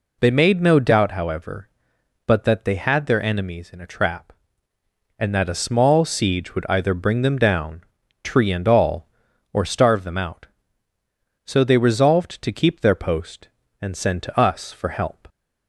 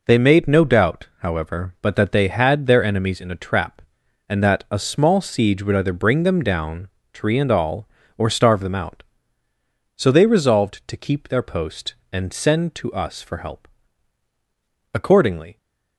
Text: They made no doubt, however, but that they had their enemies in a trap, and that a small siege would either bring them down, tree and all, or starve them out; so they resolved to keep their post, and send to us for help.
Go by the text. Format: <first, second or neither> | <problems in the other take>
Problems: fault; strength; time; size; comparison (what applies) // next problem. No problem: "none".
first | goes on to say "Accordingly"; noticeable; from 14.9 s on; 0.64 s long